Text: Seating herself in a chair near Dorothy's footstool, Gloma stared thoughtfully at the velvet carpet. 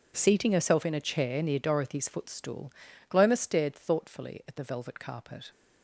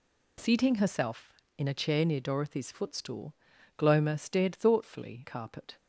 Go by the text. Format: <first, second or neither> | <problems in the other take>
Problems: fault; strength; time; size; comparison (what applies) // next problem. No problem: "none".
first | skips "at the velvet"; at 5.2 s